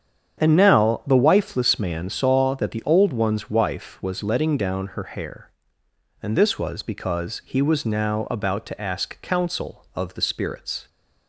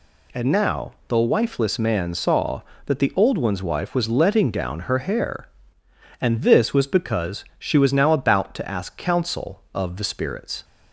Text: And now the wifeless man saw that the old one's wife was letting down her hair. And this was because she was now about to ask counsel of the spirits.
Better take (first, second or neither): second